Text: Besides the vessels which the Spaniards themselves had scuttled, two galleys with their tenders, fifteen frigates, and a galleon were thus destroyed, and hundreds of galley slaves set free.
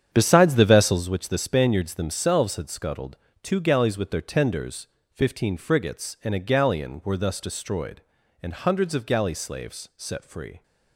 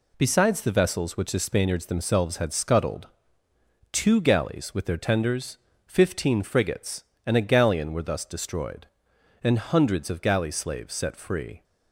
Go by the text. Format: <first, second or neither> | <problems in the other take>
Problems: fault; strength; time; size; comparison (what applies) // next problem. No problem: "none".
second | starts louder than the rest; strong; until 1.0 s; 8.5 dB